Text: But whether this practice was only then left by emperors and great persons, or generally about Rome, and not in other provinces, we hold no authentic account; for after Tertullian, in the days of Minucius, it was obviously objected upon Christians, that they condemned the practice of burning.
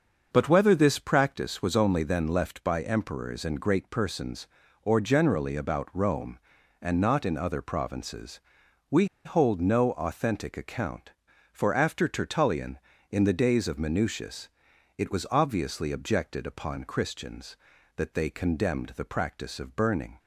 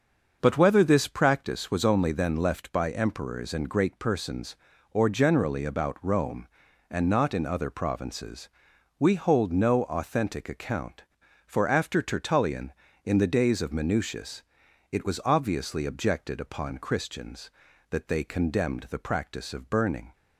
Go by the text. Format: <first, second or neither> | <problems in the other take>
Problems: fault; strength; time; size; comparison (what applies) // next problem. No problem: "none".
second | starts louder than the rest; until 1.3 s; 6.5 dB; also in the second // pauses between "we" and "hold"; slight; at 9.0 s; 0.19 s long